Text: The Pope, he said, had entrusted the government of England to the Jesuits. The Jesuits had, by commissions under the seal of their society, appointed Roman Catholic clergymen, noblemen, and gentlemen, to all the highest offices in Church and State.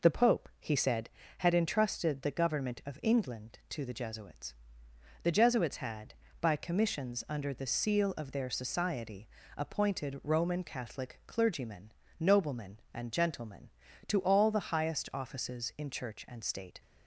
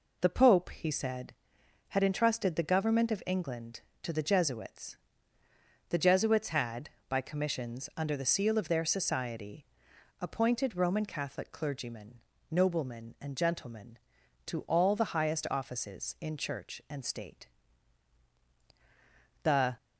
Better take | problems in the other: first | goes on to say "The"; slight; from 19.4 s on; 0.32 s long

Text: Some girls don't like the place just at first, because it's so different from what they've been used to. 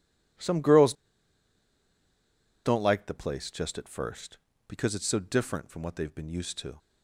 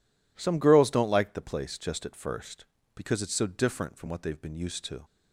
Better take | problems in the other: second | pauses between "girls" and "don't"; strong; at 0.9 s; 1.7 s long

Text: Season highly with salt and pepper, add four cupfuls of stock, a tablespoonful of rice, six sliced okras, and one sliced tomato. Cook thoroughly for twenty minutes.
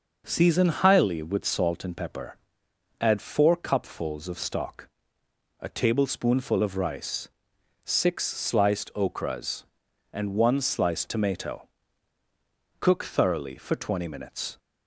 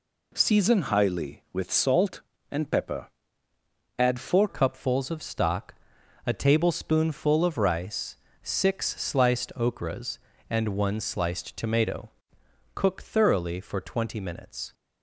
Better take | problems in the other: first | changes voice at "cupfuls"; from 4.4 s on; 10.3 s long

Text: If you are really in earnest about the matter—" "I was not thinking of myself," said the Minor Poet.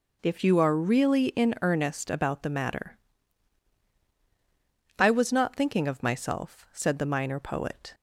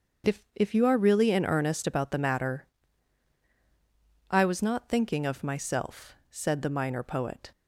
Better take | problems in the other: first | starts louder than the rest; until 1.3 s; 7 dB // says "If" twice; at 0.5 s

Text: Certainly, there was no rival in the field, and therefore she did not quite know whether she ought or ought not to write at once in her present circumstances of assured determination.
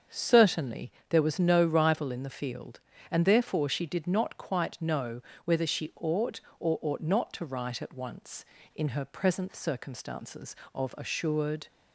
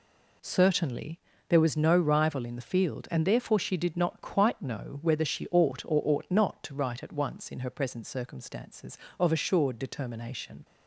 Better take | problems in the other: second | starts louder than the rest; until 1.3 s; 7 dB // pauses between "know" and "whether"; slight; at 5.1 s; 0.24 s long // stops before "determination"; at 11.6 s

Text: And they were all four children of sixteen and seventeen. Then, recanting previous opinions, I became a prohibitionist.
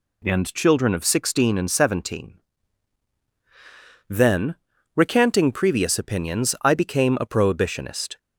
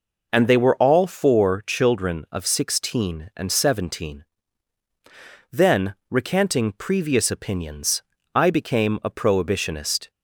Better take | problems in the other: second | skips "they were all four"; at 0.5 s

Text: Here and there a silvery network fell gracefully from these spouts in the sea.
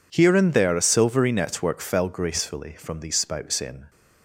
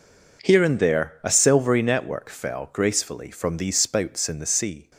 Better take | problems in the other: second | stops before "the sea"; at 3.8 s

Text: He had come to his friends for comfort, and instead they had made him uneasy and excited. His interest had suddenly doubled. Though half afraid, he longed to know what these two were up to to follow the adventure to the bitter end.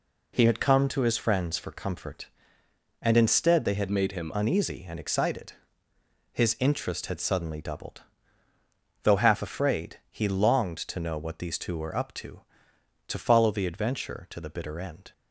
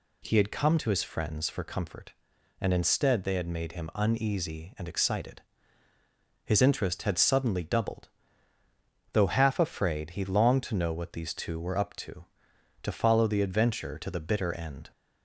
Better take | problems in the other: second | changes voice from "made" to "him"; from 3.9 to 4.3 s; 0.4 s long

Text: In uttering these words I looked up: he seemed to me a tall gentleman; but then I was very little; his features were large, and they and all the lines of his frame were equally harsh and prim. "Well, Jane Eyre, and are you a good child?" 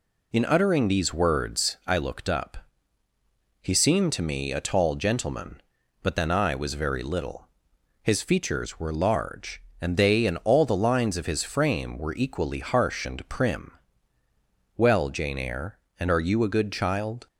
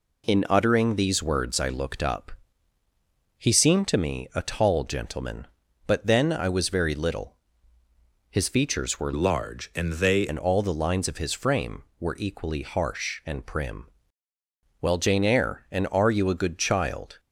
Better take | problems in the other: first | changes voice from "large" to "they"; from 9.1 to 10.2 s; 1.1 s long

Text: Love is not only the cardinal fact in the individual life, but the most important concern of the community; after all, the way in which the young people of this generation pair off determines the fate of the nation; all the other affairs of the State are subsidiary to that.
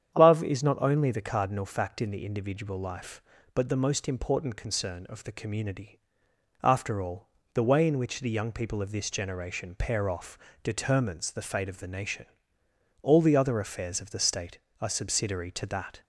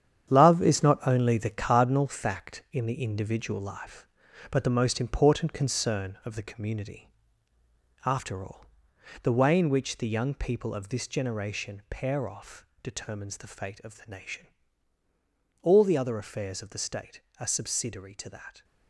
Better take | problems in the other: first | gets quieter; strong; throughout; 9 dB // starts louder than the rest; strong; until 1.3 s; 9 dB; strong in the first // pauses between "off" and "determines"; slight; at 12.6 s; 0.16 s long; slight in the first

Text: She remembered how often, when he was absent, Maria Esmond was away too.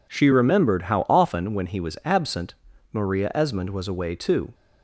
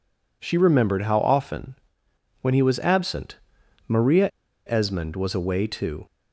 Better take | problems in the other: first | pauses between "Maria" and "Esmond"; at 4.2 s; 0.37 s long

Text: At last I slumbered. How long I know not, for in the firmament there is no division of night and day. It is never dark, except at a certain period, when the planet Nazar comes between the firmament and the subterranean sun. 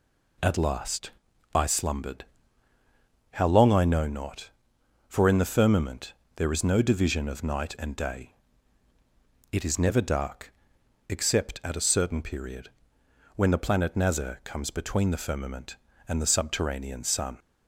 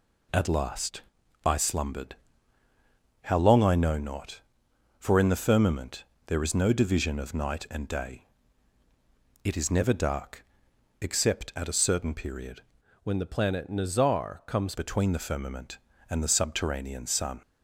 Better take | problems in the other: first | pauses between "last" and "I"; at 1.0 s; 0.42 s long; also in the first // pauses between "firmament" and "there"; slight; at 6.0 s; 0.24 s long; slight in the first // changes voice from "when" to "comes"; from 13.0 to 14.7 s; 1.7 s long

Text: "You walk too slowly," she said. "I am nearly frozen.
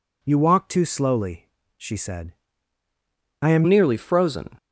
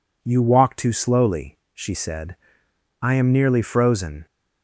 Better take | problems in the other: second | changes voice at "nearly"; from 3.6 s on; 0.9 s long

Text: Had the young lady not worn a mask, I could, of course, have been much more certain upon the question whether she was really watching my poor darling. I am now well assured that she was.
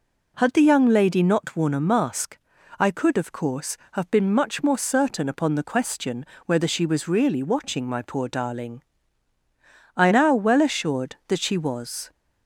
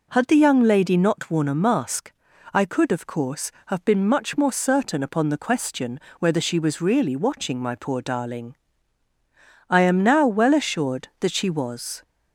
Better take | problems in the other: second | pauses between "question" and "whether"; slight; at 6.2 s; 0.20 s long; slight in the second // skips "am"; at 10.0 s

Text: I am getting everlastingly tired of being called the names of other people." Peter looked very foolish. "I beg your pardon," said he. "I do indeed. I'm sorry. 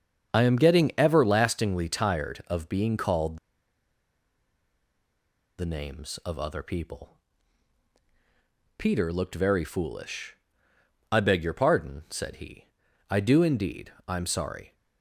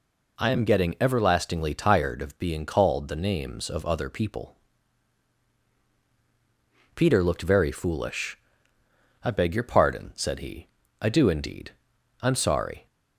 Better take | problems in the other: second | starts louder than the rest; until 1.3 s; 7 dB // pauses between "called" and "the"; strong; at 3.3 s; 2.2 s long

